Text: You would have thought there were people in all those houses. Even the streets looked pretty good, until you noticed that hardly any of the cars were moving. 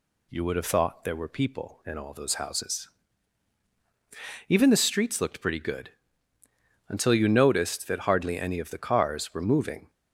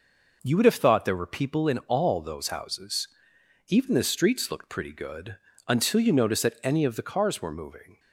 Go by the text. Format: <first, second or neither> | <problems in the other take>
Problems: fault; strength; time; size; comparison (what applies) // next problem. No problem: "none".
first | skips "hardly"; at 6.6 s